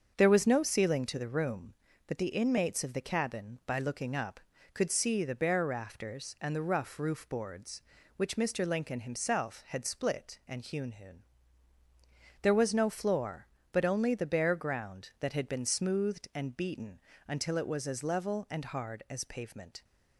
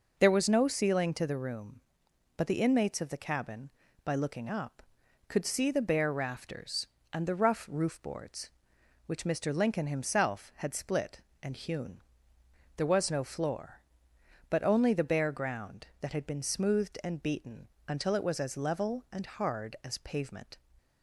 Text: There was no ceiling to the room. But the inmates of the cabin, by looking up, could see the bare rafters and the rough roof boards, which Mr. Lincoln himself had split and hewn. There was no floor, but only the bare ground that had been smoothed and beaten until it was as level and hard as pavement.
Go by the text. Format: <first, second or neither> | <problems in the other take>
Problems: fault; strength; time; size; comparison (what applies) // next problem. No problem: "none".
second | starts louder than the rest; until 1.1 s; 6.5 dB // says "hewn" twice; at 10.9 s // pauses between "beaten" and "until"; slight; at 16.9 s; 0.26 s long; slight in the second